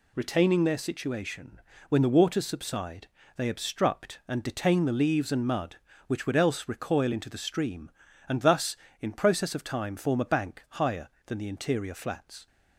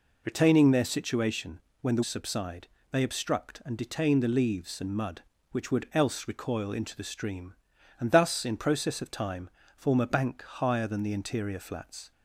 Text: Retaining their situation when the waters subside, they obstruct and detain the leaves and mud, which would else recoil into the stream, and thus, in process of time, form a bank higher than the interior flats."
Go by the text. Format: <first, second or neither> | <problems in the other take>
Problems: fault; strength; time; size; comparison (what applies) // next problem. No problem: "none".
first | pauses between "situation" and "when"; slight; at 1.5 s; 0.20 s long; slight in the first // skips "waters"; at 2.0 s